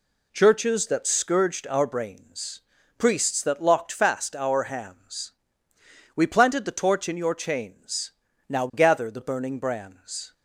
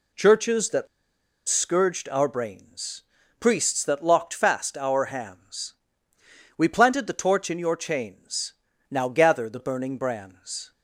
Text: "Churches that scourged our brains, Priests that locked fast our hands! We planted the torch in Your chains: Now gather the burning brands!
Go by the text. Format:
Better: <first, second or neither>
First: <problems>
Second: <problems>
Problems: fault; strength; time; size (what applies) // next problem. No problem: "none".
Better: first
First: none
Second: pauses between "that" and "scourged"; noticeable; at 0.8 s; 0.61 s long